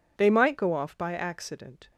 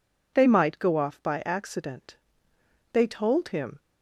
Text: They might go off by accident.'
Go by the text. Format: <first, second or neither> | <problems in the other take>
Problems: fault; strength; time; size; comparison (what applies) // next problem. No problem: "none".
first | goes on to say "They told him"; noticeable; from 2.9 s on; 0.88 s long